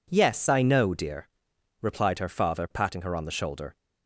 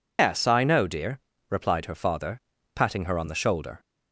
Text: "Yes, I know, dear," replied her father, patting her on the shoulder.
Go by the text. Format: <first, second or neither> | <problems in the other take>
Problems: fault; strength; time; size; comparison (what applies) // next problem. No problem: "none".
first | loses the start of "Yes"; at 0.1 s; 140 ms